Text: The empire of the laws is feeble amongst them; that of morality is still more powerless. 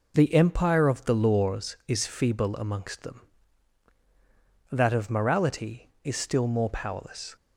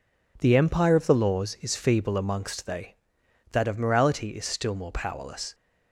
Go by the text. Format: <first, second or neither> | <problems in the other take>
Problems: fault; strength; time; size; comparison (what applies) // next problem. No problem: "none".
first | says "they" for "them"; at 2.6 s